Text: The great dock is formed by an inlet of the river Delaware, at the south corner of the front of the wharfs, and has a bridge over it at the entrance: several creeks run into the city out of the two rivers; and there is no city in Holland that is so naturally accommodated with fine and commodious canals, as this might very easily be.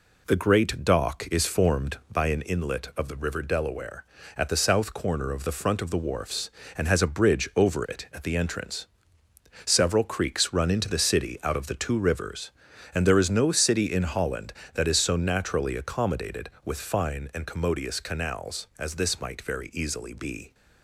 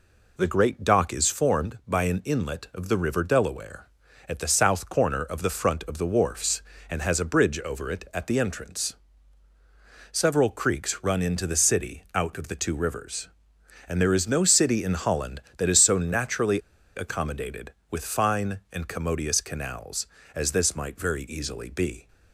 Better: first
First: none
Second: pauses between "naturally" and "accommodated"; slight; at 16.6 s; 0.35 s long

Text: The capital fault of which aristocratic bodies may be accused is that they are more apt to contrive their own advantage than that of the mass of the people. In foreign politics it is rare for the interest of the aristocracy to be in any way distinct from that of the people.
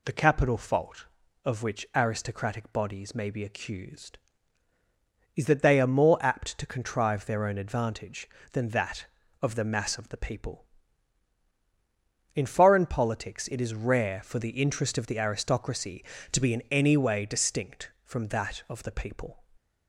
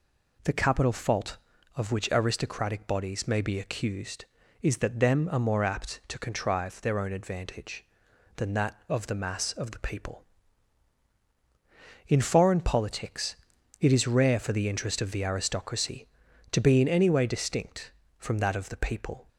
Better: first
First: none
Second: says "them" for "they"; at 4.9 s // pauses between "politics" and "it"; noticeable; at 13.3 s; 0.46 s long

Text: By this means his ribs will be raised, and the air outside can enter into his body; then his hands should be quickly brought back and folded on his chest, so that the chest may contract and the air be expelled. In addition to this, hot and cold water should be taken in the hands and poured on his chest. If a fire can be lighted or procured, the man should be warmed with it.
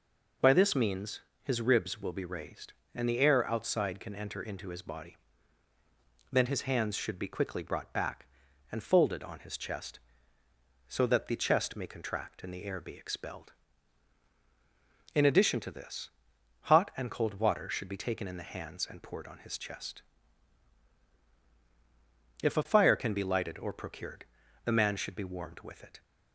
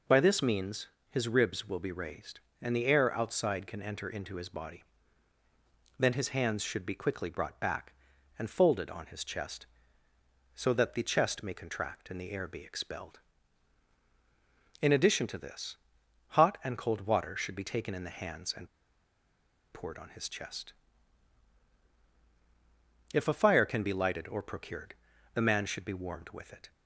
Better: first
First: pauses between "means" and "his"; slight; at 1.1 s; 0.24 s long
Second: pauses between "means" and "his"; slight; at 0.8 s; 0.24 s long // pauses between "and" and "poured"; at 18.6 s; 1.0 s long

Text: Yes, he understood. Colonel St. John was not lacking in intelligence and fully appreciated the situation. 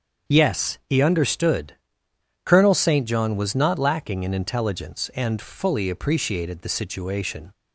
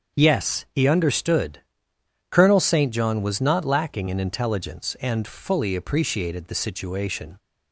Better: neither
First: starts louder than the rest; until 1.3 s; 7 dB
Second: starts louder than the rest; until 1.2 s; 7 dB

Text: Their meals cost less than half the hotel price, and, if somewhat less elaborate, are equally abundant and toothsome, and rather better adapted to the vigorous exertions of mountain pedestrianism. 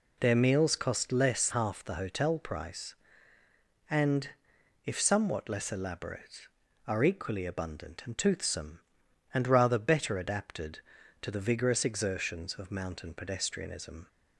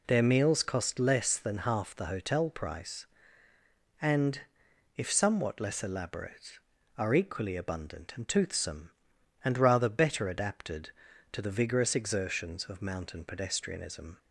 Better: second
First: skips "than"; at 1.5 s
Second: none

